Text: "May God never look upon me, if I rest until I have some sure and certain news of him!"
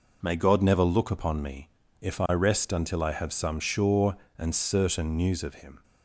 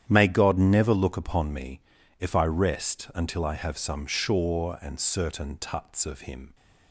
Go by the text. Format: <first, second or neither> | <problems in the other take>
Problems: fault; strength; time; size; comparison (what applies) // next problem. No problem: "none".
first | starts louder than the rest; strong; until 1.0 s; 10 dB // says "tuts" for "news"; at 5.5 s